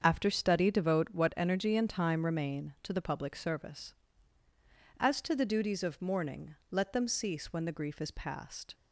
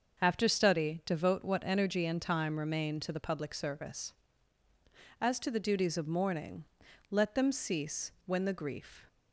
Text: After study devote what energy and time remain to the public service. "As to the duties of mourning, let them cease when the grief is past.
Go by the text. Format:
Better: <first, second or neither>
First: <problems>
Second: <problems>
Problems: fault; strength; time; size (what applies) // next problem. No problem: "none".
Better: first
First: starts louder than the rest; until 1.0 s; 7 dB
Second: starts louder than the rest; until 1.2 s; 6.5 dB // stops before "is past"; at 9.0 s